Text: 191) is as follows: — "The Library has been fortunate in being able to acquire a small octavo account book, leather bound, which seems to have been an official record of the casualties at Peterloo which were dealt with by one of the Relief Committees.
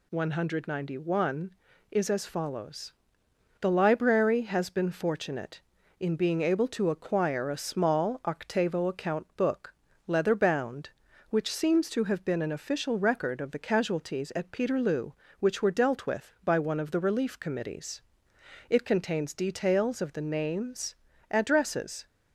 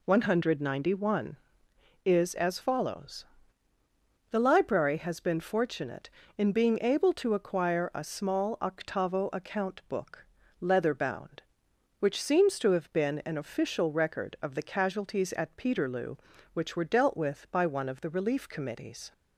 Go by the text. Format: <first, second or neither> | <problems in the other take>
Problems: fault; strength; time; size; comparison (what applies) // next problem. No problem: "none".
second | goes on to say "It contains details of the names addresses"; strong; from 18.6 s on; 3.3 s long